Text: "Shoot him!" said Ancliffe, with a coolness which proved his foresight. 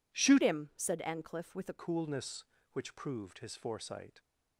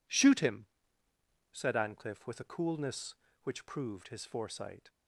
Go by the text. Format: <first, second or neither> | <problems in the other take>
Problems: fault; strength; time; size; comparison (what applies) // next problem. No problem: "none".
second | changes voice from "him" to "a"; from 0.4 to 1.7 s; 1.3 s long